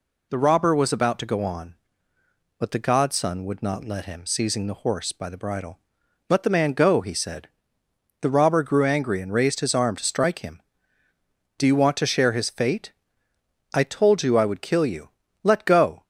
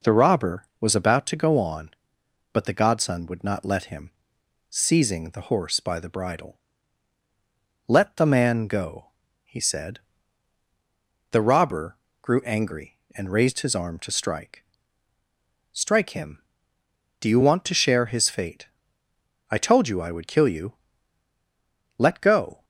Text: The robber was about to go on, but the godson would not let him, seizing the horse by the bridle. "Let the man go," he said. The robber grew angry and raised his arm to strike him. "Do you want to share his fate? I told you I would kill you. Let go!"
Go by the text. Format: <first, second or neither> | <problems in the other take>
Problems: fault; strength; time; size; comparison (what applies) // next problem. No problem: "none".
first | pauses between "robber" and "grew"; slight; at 11.9 s; 0.24 s long // says "strike" twice; at 15.7 s